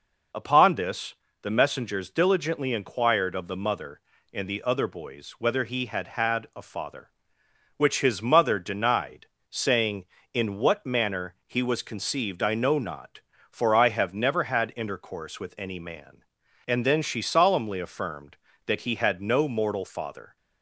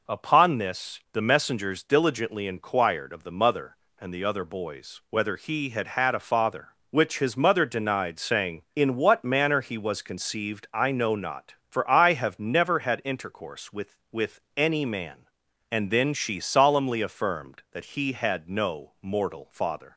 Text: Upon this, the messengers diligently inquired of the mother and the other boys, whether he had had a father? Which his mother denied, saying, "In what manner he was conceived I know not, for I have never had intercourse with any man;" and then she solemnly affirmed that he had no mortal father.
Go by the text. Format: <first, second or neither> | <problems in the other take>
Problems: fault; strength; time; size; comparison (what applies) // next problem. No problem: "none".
first | says "with" twice; at 14.1 s